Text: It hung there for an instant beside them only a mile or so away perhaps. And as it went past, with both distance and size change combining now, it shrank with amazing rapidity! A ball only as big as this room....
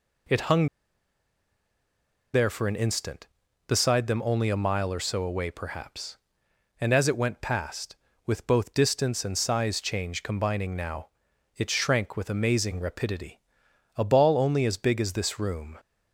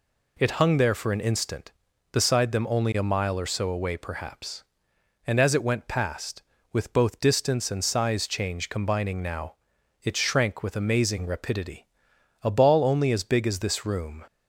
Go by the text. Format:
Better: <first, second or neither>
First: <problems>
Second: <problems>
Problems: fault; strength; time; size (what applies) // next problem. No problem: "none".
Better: second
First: pauses between "hung" and "there"; strong; at 0.6 s; 1.6 s long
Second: none